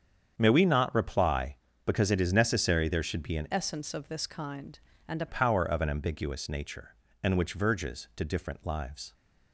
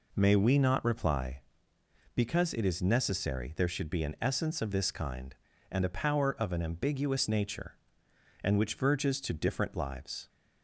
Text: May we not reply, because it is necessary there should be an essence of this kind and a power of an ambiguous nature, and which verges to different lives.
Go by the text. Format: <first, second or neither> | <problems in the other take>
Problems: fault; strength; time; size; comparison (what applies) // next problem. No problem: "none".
second | starts louder than the rest; strong; until 1.3 s; 8 dB // changes voice from "essence" to "a"; from 3.5 to 5.2 s; 1.7 s long